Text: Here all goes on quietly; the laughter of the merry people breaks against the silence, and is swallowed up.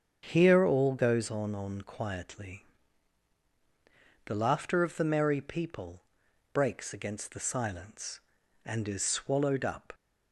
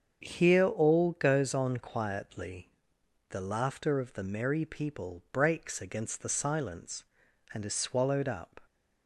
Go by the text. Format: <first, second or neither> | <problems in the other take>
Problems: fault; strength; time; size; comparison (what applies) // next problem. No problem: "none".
second | starts louder than the rest; strong; until 1.3 s; 7.5 dB; also in the second // says "on" twice; at 1.5 s // pauses between "people" and "breaks"; noticeable; at 6.0 s; 0.52 s long